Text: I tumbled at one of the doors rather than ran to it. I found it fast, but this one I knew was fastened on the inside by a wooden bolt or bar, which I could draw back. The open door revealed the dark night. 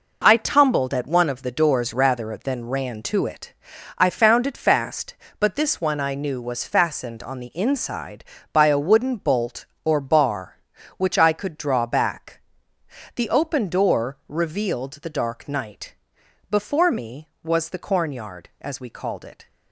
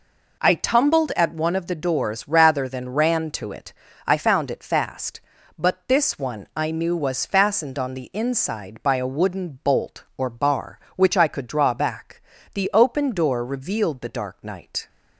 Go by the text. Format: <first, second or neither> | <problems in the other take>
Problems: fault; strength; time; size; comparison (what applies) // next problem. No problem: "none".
second | goes on to say "Before me was the cornyard as we called it"; strong; from 16.5 s on; 2.9 s long